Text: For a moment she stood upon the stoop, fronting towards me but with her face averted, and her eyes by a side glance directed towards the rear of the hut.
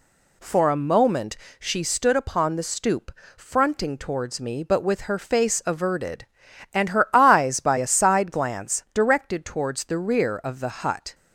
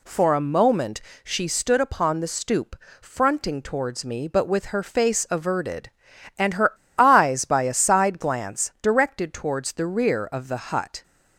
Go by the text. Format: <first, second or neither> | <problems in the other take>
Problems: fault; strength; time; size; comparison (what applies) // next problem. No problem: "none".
first | pauses between "moment" and "she"; slight; at 1.0 s; 0.24 s long; slight in the first // pauses between "her" and "eyes"; slight; at 6.7 s; 0.25 s long